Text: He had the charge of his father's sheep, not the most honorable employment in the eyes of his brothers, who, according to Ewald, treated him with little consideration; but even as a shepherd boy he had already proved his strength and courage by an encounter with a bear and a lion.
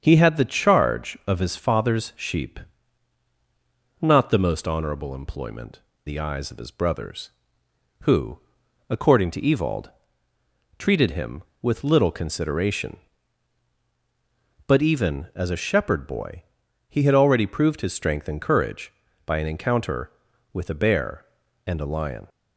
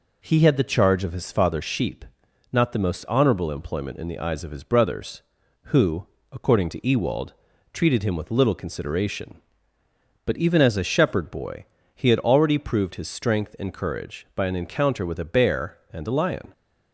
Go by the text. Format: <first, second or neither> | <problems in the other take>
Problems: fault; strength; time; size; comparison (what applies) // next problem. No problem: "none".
second | starts louder than the rest; strong; until 1.0 s; 7 dB // skips "in"; at 5.9 s // pauses between "boy" and "he"; noticeable; at 16.4 s; 0.46 s long; slight in the second